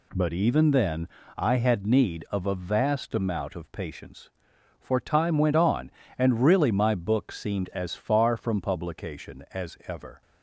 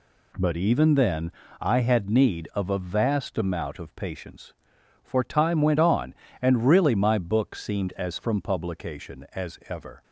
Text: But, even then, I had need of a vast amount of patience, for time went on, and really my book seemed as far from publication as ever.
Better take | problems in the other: first | skips "far"; at 8.1 s

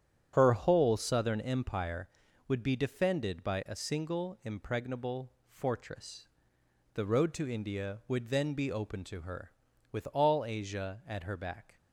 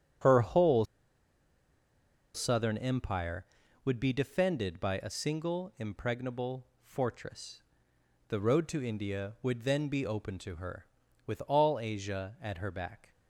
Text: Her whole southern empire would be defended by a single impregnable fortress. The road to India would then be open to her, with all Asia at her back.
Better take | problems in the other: first | starts louder than the rest; strong; until 2.7 s; 8.5 dB; strong in the first // pauses between "whole" and "southern"; strong; at 0.8 s; 1.5 s long // pauses between "impregnable" and "fortress"; slight; at 6.6 s; 0.18 s long; slight in the first

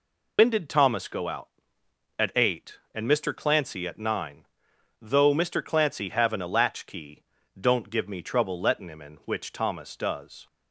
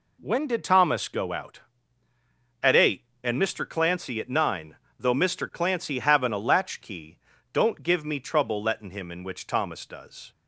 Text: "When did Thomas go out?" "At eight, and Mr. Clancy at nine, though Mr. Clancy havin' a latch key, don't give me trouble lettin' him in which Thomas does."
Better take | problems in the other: second | loses the start of "When"; at 0.3 s; 105 ms

